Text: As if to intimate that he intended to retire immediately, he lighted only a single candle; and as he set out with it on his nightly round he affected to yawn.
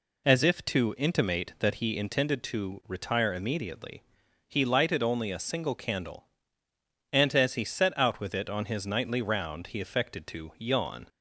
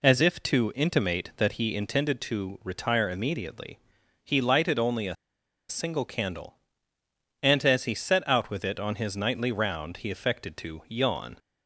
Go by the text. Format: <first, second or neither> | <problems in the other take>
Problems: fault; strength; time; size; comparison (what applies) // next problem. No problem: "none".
first | pauses between "a" and "single"; noticeable; at 5.1 s; 0.54 s long